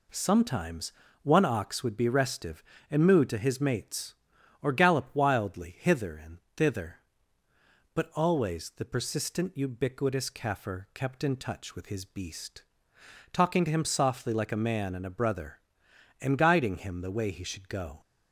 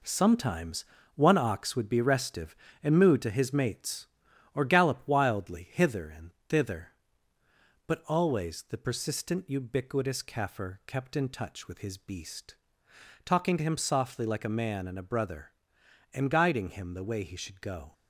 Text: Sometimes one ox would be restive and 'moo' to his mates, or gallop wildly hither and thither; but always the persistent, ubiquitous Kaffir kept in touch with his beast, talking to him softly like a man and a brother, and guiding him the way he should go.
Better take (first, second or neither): first